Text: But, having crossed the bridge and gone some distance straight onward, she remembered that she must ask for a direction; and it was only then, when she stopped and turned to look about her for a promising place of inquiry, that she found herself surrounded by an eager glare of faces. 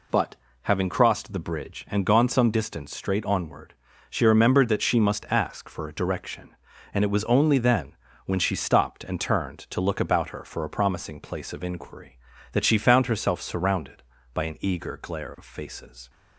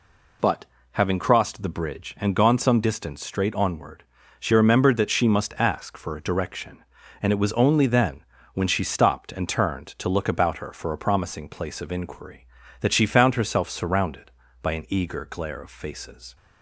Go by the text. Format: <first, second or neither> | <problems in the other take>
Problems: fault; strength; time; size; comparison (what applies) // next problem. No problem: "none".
neither | none